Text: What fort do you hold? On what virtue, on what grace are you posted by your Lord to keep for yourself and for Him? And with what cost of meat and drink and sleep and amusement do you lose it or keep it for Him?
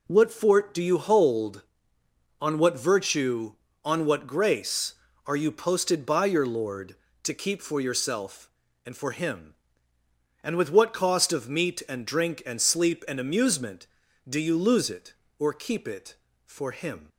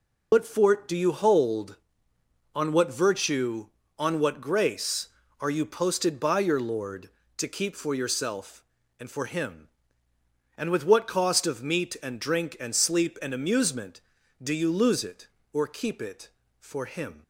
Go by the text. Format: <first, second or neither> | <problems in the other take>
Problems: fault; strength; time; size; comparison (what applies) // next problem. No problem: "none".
first | loses the start of "What"; at 0.3 s; 100 ms